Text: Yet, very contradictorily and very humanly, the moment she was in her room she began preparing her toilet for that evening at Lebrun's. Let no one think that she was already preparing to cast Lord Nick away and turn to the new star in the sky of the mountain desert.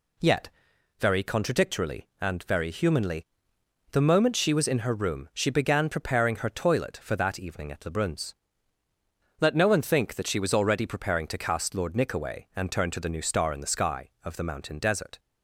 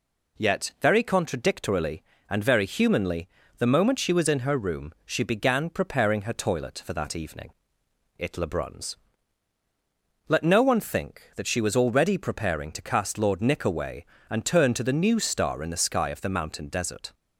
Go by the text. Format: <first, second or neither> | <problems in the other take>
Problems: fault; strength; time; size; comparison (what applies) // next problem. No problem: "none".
first | says "it" for "at"; at 8.1 s